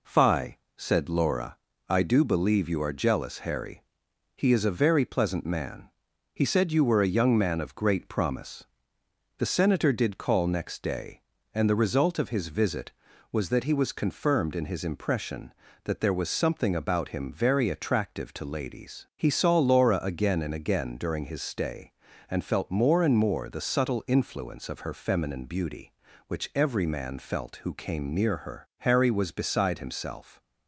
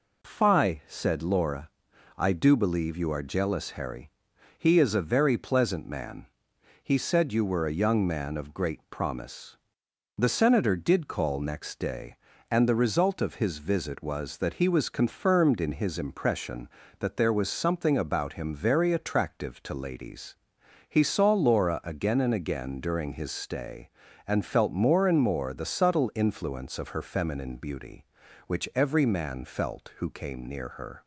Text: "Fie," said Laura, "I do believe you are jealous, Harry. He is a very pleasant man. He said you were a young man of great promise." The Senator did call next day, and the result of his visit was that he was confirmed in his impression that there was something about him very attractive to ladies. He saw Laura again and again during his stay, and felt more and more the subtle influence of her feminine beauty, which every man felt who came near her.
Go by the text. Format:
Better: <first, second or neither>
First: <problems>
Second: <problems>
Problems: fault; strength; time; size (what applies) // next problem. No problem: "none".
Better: second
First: goes on to say "Harry was beside himself"; from 28.7 s on; 1.6 s long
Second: none